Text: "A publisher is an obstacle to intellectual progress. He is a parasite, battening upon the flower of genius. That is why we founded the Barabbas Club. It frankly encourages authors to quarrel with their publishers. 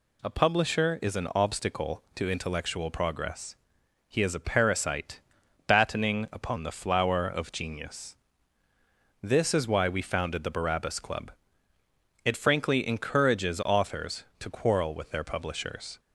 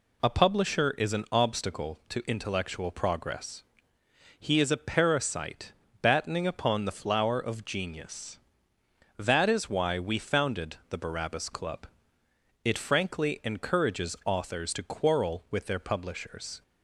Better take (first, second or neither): second